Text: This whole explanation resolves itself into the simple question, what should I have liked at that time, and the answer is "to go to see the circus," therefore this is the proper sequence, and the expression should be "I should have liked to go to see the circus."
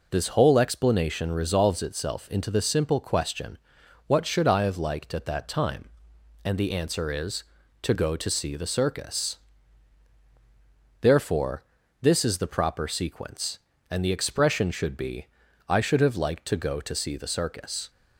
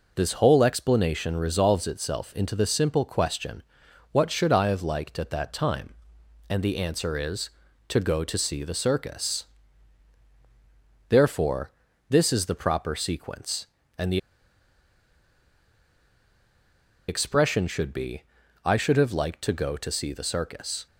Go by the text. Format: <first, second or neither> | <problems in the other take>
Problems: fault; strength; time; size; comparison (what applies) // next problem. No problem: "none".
first | pauses between "therefore" and "this"; at 11.6 s; 0.38 s long; also in the first // pauses between "the" and "expression"; strong; at 14.1 s; 2.9 s long // pauses between "be" and "I"; at 18.2 s; 0.40 s long; also in the first